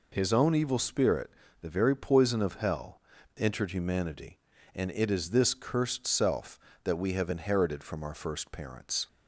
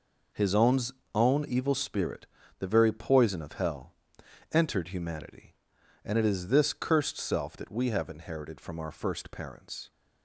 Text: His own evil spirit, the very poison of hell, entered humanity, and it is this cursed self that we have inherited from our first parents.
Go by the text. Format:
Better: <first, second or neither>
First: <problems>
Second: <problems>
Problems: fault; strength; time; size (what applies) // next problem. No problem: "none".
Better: first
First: none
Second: says "own" twice; at 1.1 s